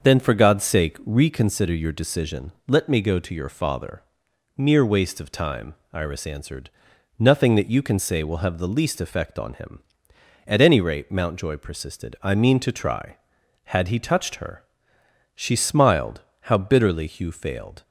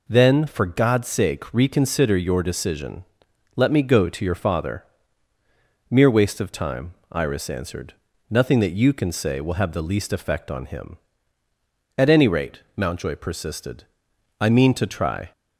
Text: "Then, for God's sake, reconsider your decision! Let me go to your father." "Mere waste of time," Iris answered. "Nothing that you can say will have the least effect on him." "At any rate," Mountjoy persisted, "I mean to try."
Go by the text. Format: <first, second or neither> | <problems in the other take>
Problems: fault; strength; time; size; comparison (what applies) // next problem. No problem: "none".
second | starts louder than the rest; until 1.0 s; 6.5 dB // goes on to say "Had he touched her She smiled how bitterly Hugh failed"; strong; from 13.6 s on; 4.1 s long